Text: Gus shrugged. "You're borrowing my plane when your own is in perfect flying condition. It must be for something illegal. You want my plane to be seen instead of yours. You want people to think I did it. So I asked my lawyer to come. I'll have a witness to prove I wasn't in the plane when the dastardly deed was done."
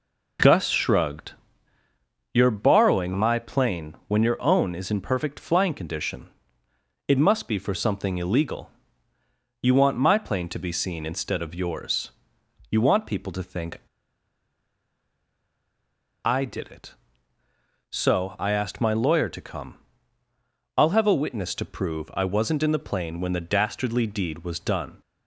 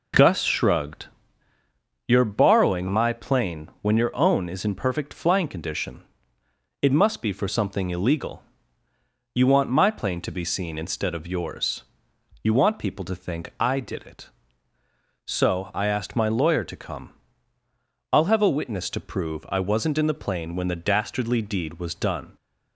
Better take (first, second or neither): second